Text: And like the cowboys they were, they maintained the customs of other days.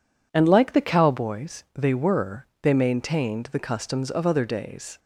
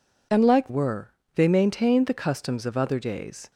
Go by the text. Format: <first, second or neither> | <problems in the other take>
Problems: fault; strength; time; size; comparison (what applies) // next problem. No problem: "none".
first | skips "the cowboys they"; at 0.6 s